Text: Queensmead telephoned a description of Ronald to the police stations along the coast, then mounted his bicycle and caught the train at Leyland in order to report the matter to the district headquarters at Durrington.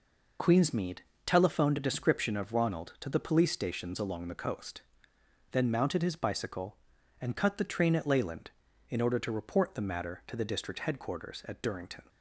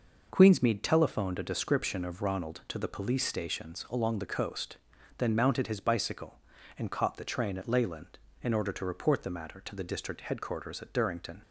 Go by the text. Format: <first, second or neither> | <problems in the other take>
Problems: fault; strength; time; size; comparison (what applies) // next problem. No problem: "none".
second | pauses between "Queensmead" and "telephoned"; slight; at 1.0 s; 0.24 s long // says "cut" for "caught"; at 7.3 s